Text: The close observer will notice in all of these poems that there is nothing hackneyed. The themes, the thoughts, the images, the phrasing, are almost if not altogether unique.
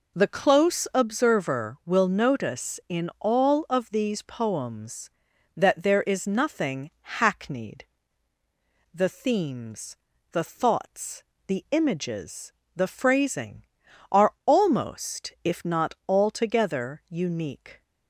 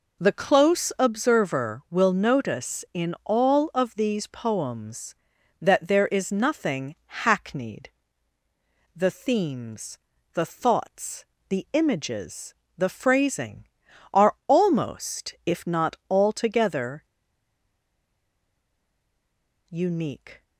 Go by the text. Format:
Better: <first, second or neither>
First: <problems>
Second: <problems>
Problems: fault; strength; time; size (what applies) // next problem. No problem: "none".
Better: first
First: pauses between "not" and "altogether"; slight; at 15.9 s; 0.16 s long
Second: pauses between "not" and "altogether"; slight; at 15.9 s; 0.16 s long // pauses between "altogether" and "unique"; strong; at 17.0 s; 2.6 s long